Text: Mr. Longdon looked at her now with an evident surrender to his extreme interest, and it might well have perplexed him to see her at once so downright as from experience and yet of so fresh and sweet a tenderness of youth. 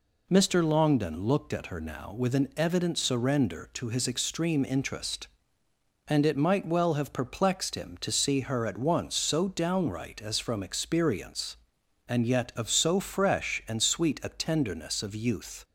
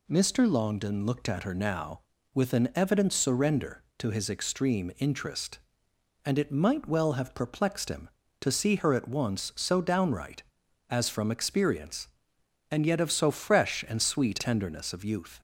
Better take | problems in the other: first | skips "a"; at 14.3 s

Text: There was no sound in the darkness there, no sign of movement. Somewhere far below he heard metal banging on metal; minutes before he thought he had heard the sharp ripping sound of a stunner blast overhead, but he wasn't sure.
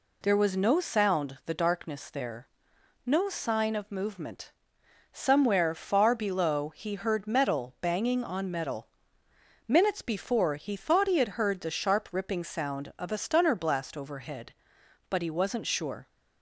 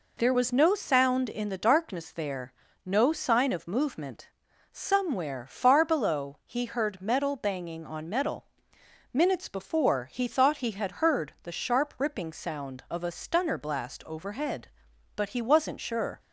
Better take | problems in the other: second | skips "in"; at 1.4 s

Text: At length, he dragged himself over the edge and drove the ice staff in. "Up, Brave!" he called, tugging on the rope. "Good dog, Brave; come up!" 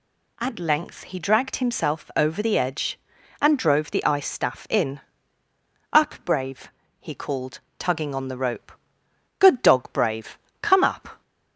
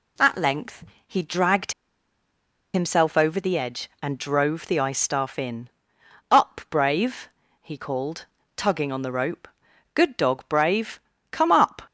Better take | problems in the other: first | pauses between "dragged" and "himself"; at 1.7 s; 1.0 s long

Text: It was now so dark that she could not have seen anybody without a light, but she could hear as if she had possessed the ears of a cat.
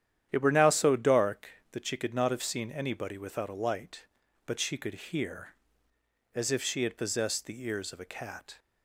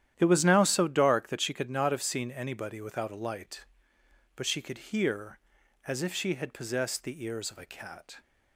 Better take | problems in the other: second | starts louder than the rest; strong; until 1.3 s; 10.5 dB; strong in the second // says "were" for "was"; at 0.4 s

